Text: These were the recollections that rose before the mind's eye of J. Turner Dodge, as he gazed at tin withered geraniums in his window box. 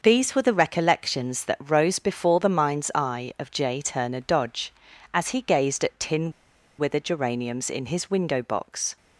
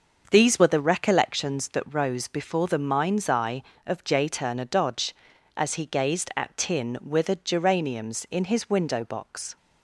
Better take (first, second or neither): second